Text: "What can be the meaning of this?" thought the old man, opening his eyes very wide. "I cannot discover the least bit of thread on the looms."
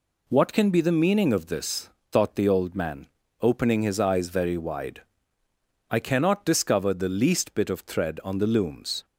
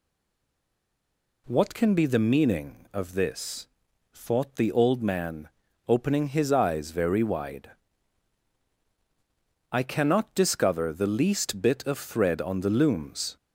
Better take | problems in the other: first | stays silent before the first word; noticeable; until 1.4 s; 1.4 s long

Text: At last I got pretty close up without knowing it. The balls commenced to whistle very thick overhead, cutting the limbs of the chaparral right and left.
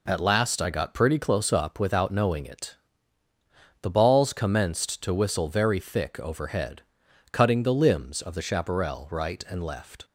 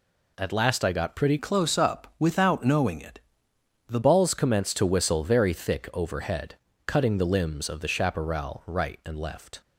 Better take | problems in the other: first | changes voice from "close" to "The"; from 1.3 to 3.9 s; 2.6 s long

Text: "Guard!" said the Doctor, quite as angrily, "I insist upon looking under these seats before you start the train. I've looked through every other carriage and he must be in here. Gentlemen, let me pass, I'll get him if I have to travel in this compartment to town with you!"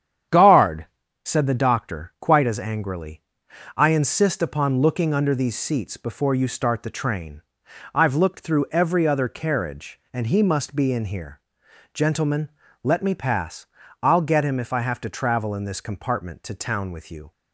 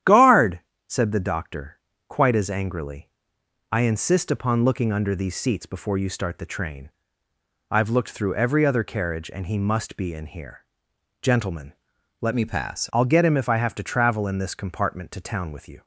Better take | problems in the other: first | starts louder than the rest; strong; until 1.3 s; 10.5 dB; strong in the first // changes voice from "me" to "pass"; from 12.3 to 12.8 s; 0.5 s long

